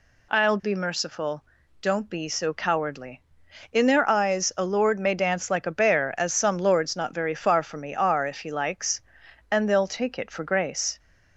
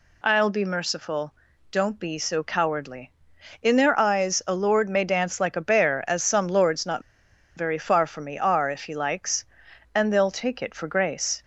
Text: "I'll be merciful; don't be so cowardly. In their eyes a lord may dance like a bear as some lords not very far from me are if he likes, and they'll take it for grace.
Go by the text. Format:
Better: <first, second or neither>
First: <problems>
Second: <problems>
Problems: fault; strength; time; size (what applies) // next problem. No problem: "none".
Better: first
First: none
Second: pauses between "not" and "very"; noticeable; at 7.0 s; 0.53 s long